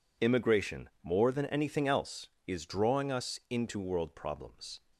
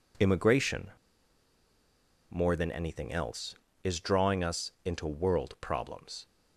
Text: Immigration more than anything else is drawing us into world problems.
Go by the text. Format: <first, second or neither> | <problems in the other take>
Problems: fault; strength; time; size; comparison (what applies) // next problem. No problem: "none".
first | pauses between "Immigration" and "more"; strong; at 0.9 s; 1.3 s long